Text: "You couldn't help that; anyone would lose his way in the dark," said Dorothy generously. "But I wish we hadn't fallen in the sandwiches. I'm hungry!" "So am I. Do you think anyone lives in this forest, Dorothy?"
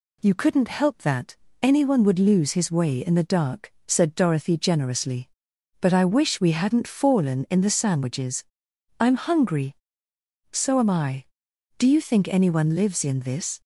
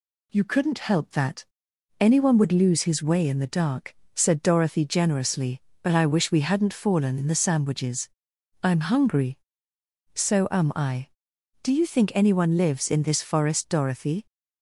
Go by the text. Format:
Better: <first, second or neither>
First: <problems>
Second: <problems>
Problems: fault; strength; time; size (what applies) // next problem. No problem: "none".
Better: second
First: stops before "forest Dorothy"; at 13.6 s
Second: none